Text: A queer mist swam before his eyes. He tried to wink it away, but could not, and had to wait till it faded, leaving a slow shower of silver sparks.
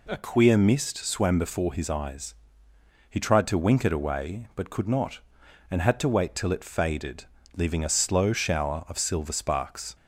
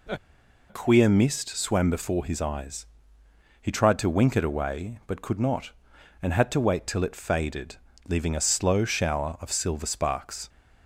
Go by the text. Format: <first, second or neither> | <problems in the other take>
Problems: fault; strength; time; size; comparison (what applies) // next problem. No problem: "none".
first | pauses between "A" and "queer"; noticeable; at 0.1 s; 0.53 s long